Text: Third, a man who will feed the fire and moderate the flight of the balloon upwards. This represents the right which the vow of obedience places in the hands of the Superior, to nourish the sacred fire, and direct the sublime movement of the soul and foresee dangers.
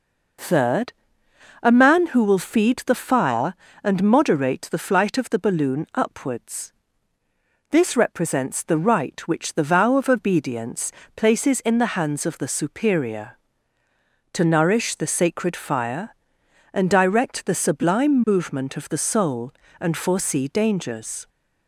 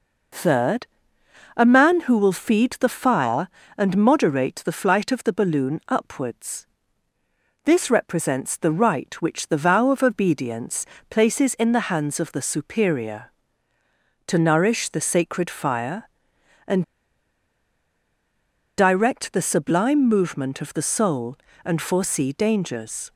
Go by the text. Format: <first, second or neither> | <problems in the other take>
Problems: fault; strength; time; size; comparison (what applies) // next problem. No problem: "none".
first | pauses between "obedience" and "places"; slight; at 10.8 s; 0.22 s long; slight in the first // pauses between "and" and "direct"; strong; at 16.8 s; 1.9 s long